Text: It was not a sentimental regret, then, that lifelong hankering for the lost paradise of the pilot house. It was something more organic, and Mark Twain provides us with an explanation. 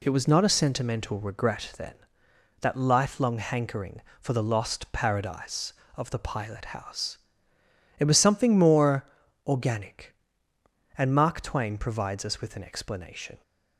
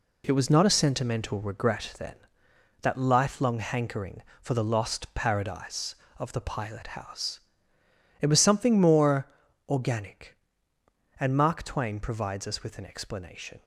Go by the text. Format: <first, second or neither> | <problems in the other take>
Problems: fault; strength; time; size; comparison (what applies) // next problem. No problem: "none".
first | gets quieter; strong; throughout; 8 dB // pauses between "more" and "organic"; at 9.2 s; 0.40 s long; also in the first